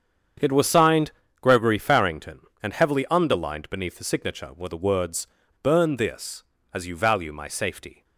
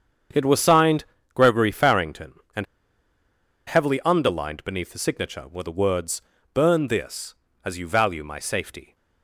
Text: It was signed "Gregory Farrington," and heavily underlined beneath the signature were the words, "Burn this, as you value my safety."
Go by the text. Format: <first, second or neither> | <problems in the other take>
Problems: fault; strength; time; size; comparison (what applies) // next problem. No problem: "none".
first | starts louder than the rest; strong; until 1.6 s; 7.5 dB; strong in the first // pauses between "signed" and "Gregory"; slight; at 1.0 s; 0.30 s long; slight in the first // pauses between "and" and "heavily"; at 2.6 s; 1.0 s long